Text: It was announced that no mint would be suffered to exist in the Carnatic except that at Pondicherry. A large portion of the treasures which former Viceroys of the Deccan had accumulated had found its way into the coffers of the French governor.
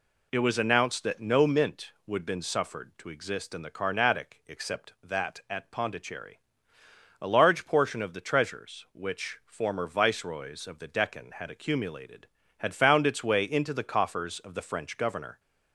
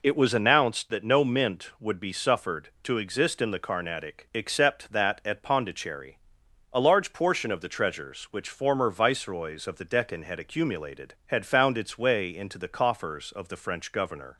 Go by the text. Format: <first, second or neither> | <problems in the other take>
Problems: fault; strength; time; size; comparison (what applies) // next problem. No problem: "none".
second | says "been" for "be"; at 2.2 s